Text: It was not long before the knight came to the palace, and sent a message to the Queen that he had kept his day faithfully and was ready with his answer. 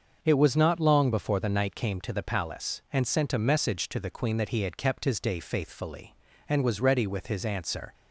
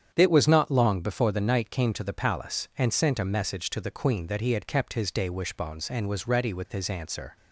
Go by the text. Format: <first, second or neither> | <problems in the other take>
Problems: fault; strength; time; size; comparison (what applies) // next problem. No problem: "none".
first | starts louder than the rest; strong; until 1.1 s; 8.5 dB; also in the first // says "wishbones" for "faithfully"; at 5.3 s